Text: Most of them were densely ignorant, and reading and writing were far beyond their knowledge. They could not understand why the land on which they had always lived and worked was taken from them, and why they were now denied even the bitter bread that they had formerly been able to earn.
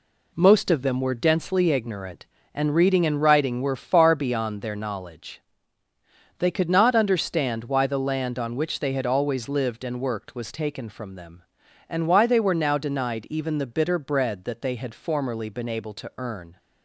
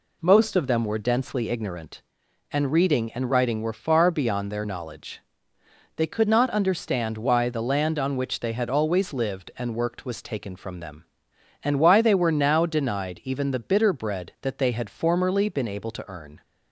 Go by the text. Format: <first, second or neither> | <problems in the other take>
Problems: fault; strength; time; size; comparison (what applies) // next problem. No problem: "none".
neither | none